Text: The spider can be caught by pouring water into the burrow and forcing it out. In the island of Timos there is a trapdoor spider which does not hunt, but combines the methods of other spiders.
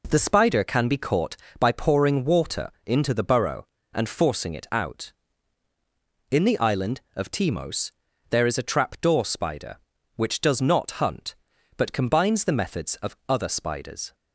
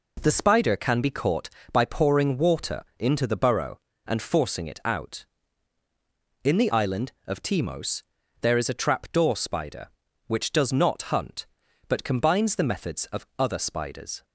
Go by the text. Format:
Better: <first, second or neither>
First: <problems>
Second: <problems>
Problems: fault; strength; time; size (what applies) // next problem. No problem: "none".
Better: neither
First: pauses between "water" and "into"; slight; at 2.6 s; 0.16 s long // pauses between "Timos" and "there"; at 7.8 s; 0.40 s long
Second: pauses between "water" and "into"; slight; at 2.8 s; 0.16 s long // pauses between "Timos" and "there"; at 8.0 s; 0.40 s long